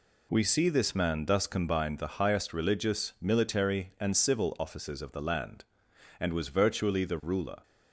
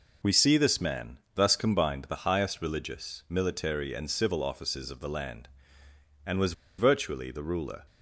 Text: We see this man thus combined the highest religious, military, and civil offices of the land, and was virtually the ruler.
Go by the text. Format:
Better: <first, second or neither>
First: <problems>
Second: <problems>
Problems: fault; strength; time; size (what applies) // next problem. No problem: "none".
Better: first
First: none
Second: pauses between "man" and "thus"; slight; at 1.1 s; 0.16 s long // pauses between "was" and "virtually"; slight; at 6.5 s; 0.26 s long